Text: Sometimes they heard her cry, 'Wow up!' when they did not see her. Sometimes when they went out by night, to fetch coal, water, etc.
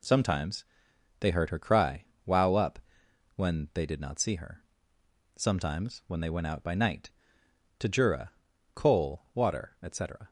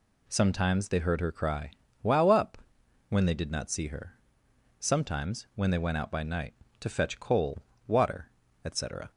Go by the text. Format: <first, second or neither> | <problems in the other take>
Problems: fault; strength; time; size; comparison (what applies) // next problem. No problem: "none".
second | pauses between "Sometimes" and "they"; noticeable; at 0.6 s; 0.56 s long // says "jura" for "fetch"; at 7.8 s